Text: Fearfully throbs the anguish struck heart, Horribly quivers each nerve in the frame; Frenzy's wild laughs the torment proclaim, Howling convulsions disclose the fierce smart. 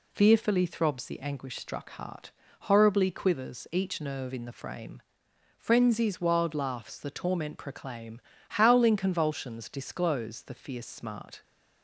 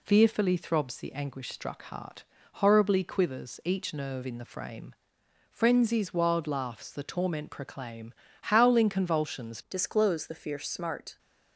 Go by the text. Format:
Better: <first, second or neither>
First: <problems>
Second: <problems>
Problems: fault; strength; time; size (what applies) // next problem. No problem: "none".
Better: first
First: none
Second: changes voice at "disclose"; from 9.6 s on; 1.5 s long